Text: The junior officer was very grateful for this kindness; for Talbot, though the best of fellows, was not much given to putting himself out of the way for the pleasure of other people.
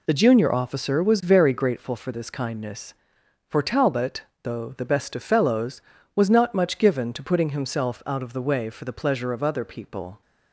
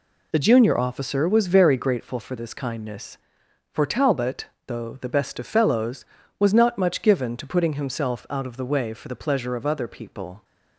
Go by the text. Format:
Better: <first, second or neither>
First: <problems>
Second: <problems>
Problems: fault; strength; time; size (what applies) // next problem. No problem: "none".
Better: neither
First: none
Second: none